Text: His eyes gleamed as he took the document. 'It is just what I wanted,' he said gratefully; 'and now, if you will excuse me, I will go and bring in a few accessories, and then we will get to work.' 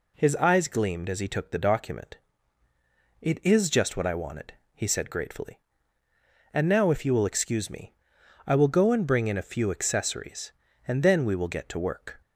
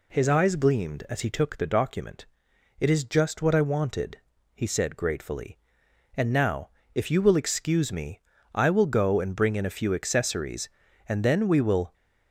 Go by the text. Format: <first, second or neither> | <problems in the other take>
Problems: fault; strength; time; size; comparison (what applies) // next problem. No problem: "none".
first | stops before "get to work"; at 11.9 s